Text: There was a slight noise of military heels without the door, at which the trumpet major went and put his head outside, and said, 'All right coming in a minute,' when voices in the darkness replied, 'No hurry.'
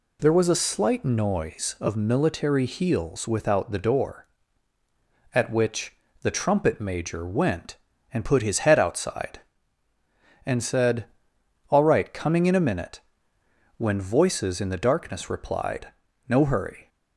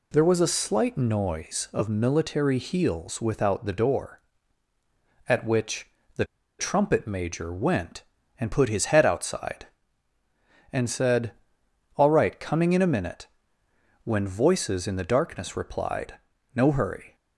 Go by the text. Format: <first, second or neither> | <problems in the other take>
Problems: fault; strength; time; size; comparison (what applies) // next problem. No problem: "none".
first | pauses between "which" and "the"; slight; at 5.8 s; 0.28 s long; slight in the first // pauses between "the" and "trumpet"; slight; at 6.2 s; 0.34 s long